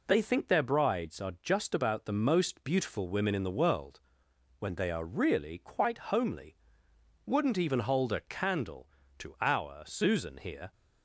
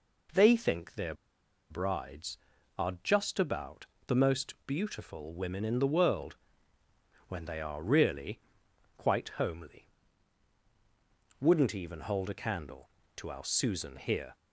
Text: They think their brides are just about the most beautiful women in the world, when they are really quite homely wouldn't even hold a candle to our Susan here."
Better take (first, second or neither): first